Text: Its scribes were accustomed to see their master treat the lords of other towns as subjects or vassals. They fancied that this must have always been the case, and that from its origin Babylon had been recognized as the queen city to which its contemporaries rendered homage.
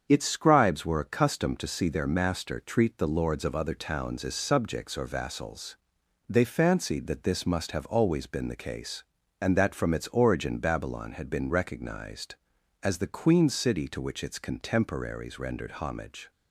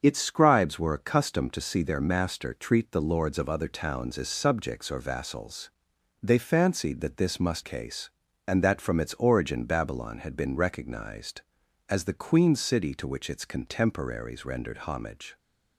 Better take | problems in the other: first | starts louder than the rest; until 1.0 s; 7 dB; strong in the first // skips "have always been the"; at 7.6 s

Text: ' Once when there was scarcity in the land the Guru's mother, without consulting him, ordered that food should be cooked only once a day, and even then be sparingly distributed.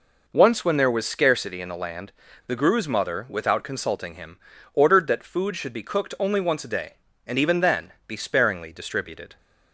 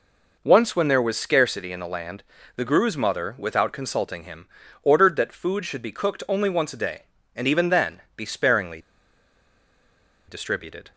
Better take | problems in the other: first | pauses between "land" and "the"; slight; at 2.2 s; 0.32 s long; slight in the first // pauses between "sparingly" and "distributed"; strong; at 8.7 s; 1.4 s long

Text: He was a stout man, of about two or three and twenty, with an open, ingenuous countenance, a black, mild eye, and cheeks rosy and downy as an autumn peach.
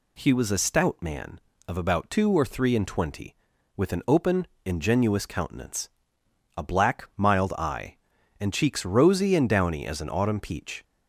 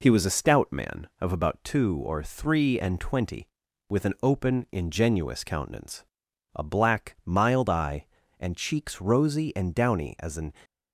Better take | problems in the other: first | stops before "autumn peach"; at 10.6 s

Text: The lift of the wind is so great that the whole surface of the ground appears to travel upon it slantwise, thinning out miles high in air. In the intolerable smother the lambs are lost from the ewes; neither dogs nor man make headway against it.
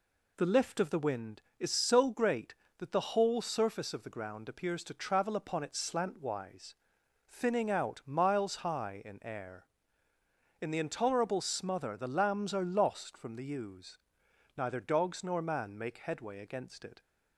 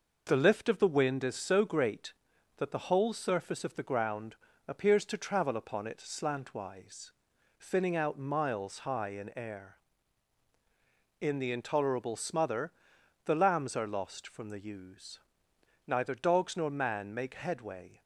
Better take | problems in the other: first | pauses between "ground" and "appears"; slight; at 4.3 s; 0.32 s long // pauses between "smother" and "the"; noticeable; at 12.7 s; 0.52 s long // stops before "against it"; at 18.0 s

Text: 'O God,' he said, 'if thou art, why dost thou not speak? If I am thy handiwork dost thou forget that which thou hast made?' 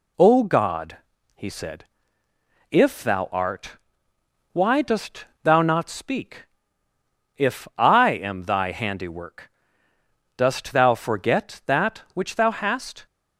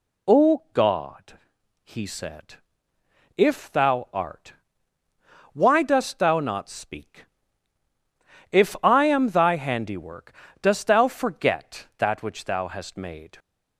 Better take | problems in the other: second | pauses between "dost" and "thou"; slight; at 5.2 s; 0.16 s long // pauses between "handiwork" and "dost"; noticeable; at 9.4 s; 0.86 s long; slight in the second // stops before "made"; at 13.0 s

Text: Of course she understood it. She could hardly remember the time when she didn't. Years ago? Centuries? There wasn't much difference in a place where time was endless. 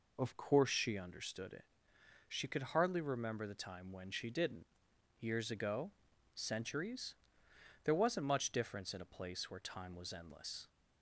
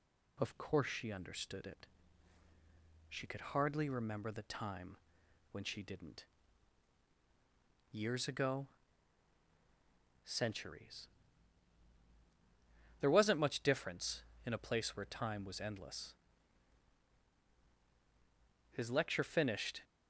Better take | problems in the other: first | pauses between "time" and "when"; noticeable; at 4.9 s; 0.54 s long // goes on to say "His lecture finished"; noticeable; from 18.7 s on; 1.1 s long

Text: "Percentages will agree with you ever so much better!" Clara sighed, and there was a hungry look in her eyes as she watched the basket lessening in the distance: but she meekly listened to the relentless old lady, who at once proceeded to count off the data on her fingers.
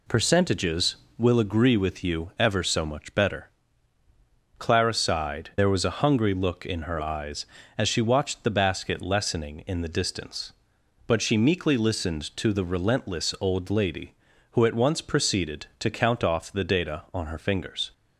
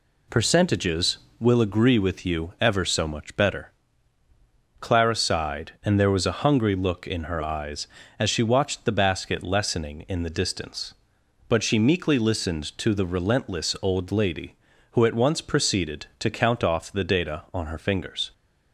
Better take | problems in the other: second | skips "and"; at 5.5 s

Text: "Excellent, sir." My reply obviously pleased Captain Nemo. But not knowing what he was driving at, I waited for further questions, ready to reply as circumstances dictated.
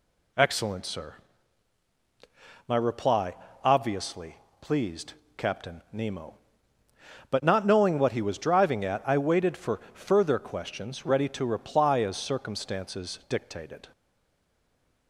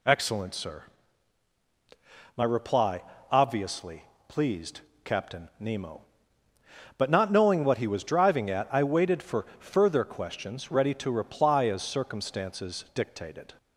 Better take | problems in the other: second | pauses between "reply" and "obviously"; slight; at 3.3 s; 0.28 s long; slight in the second // pauses between "obviously" and "pleased"; slight; at 4.3 s; 0.24 s long; slight in the second // pauses between "pleased" and "Captain"; slight; at 5.1 s; 0.24 s long; slight in the second // stays silent after the last word; from 13.9 s on; 1.1 s long

